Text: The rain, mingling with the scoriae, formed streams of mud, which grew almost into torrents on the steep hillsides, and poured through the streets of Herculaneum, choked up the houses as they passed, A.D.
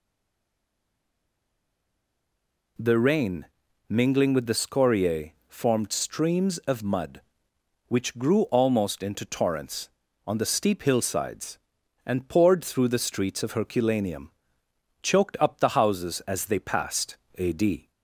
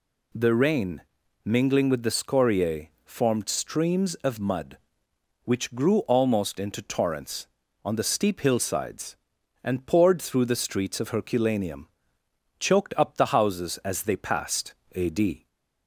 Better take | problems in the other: second | stays silent before the first word; strong; until 2.7 s; 2.7 s long

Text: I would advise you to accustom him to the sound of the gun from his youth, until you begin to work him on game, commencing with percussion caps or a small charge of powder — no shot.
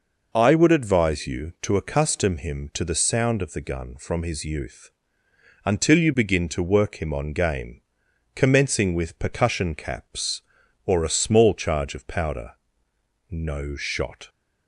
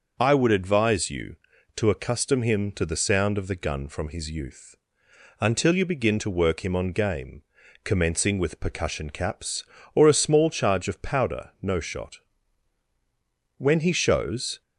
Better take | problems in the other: first | starts louder than the rest; noticeable; until 1.1 s; 6 dB // goes on to say "When he shows"; noticeable; from 13.5 s on; 1.0 s long

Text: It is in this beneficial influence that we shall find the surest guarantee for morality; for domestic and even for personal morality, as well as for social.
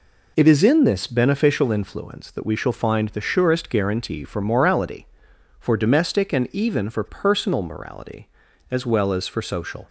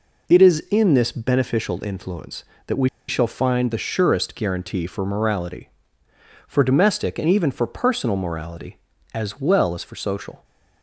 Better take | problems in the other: first | pauses between "we" and "shall"; slight; at 2.8 s; 0.20 s long

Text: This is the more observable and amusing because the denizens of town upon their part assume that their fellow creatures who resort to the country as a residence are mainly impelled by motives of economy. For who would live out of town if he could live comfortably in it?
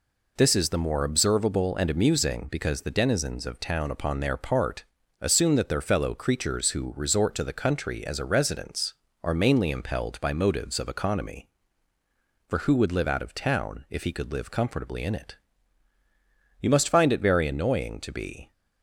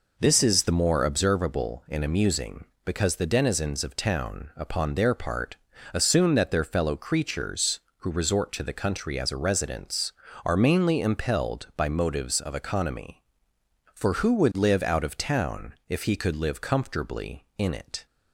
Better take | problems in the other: second | pauses between "part" and "assume"; slight; at 4.8 s; 0.34 s long; slight in the second // goes on to say "You must find it very annoying to be"; strong; from 16.6 s on; 1.9 s long

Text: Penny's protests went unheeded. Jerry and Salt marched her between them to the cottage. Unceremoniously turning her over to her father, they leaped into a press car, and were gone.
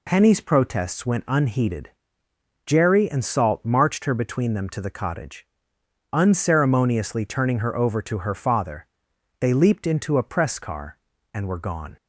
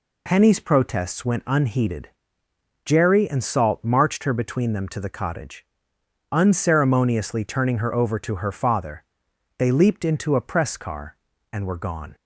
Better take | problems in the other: neither | none

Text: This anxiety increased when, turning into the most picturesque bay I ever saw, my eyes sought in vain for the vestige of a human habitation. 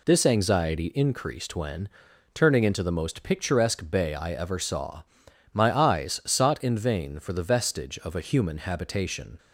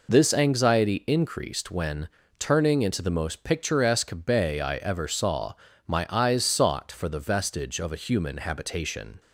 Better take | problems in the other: first | skips "in vain"; at 6.8 s

